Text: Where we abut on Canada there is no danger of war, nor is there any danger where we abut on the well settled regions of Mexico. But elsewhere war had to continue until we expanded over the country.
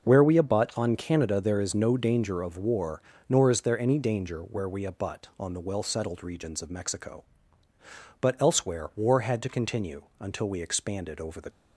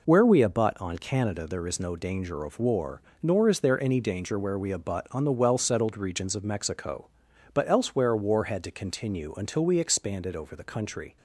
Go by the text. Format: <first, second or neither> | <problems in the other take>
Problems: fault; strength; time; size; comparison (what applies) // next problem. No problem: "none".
second | pauses between "continue" and "until"; slight; at 10.0 s; 0.18 s long // stops before "country"; at 11.4 s